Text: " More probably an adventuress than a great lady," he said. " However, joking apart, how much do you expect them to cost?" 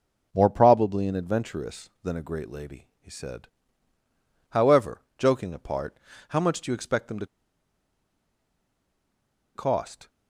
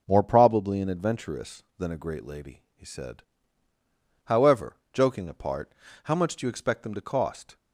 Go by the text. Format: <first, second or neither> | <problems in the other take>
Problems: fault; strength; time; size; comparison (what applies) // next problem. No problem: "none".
second | pauses between "to" and "cost"; strong; at 7.2 s; 2.2 s long